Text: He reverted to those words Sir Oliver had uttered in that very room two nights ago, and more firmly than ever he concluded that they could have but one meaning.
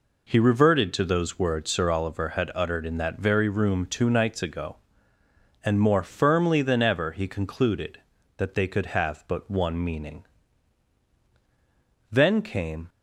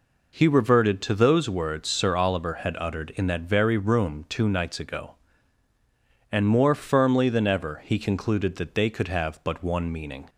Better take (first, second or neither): second